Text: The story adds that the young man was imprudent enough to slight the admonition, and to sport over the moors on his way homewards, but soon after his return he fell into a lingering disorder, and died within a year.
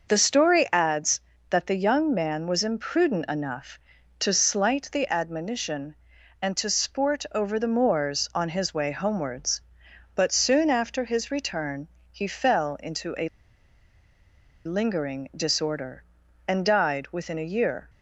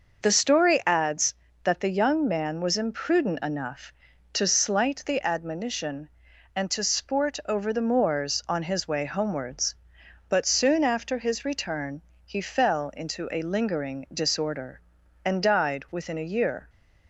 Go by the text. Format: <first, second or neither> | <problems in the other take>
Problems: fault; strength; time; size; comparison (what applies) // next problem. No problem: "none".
second | pauses between "return" and "he"; slight; at 11.8 s; 0.20 s long; slight in the second // pauses between "a" and "lingering"; strong; at 13.2 s; 1.3 s long